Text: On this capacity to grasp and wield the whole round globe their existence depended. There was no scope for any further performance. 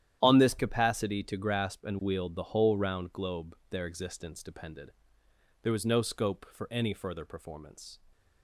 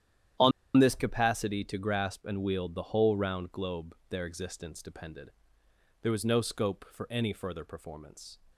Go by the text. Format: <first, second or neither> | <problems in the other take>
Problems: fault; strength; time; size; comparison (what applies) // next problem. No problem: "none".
first | starts louder than the rest; strong; until 1.6 s; 10.5 dB; strong in the first // pauses between "On" and "this"; slight; at 0.5 s; 0.26 s long